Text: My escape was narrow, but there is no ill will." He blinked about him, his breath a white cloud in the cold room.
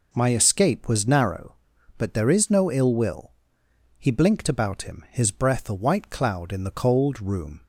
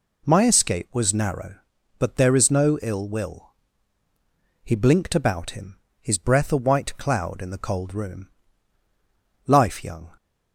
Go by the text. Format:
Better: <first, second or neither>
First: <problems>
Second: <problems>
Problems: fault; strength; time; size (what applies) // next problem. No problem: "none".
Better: first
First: none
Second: goes on to say "Life young"; noticeable; from 9.4 s on; 0.66 s long